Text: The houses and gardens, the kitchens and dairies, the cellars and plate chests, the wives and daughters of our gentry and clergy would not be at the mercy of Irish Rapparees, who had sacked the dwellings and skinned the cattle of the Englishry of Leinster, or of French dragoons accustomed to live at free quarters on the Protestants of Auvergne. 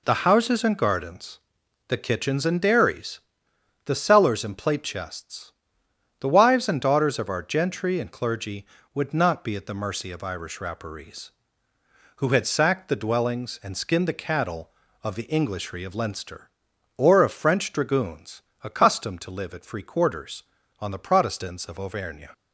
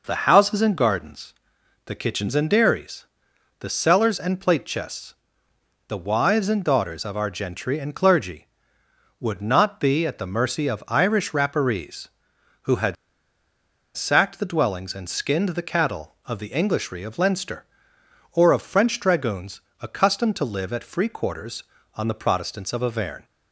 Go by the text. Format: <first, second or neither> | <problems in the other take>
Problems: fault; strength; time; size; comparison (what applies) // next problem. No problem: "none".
first | pauses between "had" and "sacked"; at 12.9 s; 1.0 s long // pauses between "dragoons" and "accustomed"; slight; at 19.6 s; 0.20 s long; slight in the first